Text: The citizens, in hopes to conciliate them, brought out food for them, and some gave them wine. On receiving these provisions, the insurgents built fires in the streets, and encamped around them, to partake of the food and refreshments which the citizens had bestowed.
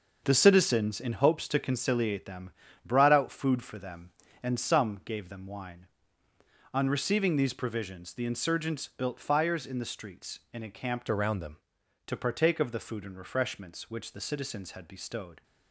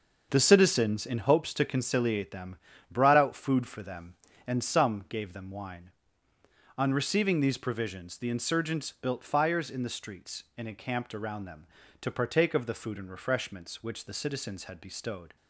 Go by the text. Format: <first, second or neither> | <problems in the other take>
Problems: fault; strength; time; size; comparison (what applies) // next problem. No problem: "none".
second | starts louder than the rest; until 1.2 s; 6 dB // changes voice from "around" to "them"; from 11.1 to 11.5 s; 0.4 s long